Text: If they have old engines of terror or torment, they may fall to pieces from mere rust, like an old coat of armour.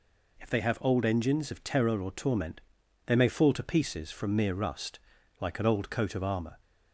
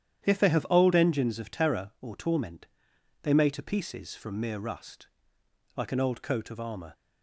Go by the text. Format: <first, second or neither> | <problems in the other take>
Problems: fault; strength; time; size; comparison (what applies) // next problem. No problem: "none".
first | starts louder than the rest; strong; until 1.2 s; 10 dB // skips "fall"; at 3.4 s